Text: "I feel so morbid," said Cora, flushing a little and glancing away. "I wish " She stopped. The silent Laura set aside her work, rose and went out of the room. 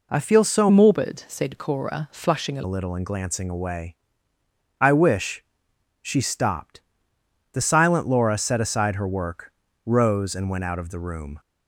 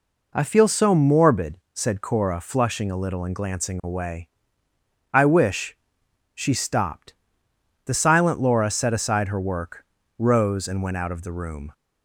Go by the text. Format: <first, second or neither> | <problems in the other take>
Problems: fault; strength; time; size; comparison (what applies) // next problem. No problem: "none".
second | changes voice from "morbid" to "a"; from 0.7 to 2.6 s; 1.9 s long